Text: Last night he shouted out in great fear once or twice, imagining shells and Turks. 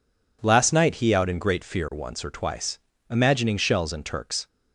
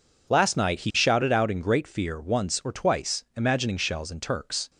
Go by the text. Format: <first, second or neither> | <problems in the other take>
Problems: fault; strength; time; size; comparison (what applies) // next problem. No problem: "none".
second | skips "shouted"; at 1.1 s